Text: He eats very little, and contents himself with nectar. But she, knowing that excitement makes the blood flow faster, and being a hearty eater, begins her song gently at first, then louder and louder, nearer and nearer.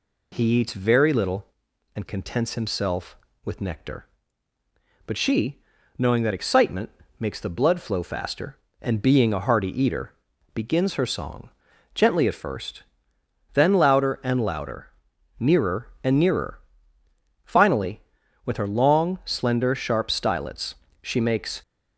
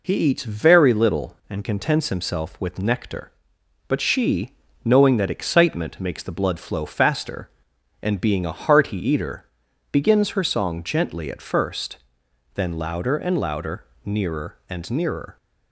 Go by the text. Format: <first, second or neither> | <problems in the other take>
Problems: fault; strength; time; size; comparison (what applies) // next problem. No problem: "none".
second | pauses between "excitement" and "makes"; slight; at 6.8 s; 0.32 s long // pauses between "song" and "gently"; at 11.4 s; 0.44 s long // goes on to say "Finally with her long slender sharp stylets she makes"; strong; from 17.4 s on; 4.1 s long